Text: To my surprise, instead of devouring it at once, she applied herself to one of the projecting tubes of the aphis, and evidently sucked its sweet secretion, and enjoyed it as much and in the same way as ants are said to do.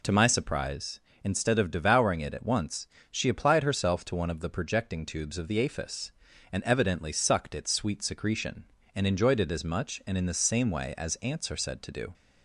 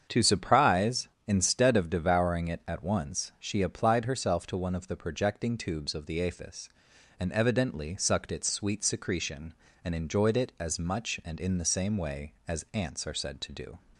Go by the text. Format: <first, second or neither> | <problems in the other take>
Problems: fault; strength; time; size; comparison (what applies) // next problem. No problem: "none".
first | starts louder than the rest; strong; until 1.2 s; 7.5 dB // skips "my"; at 0.2 s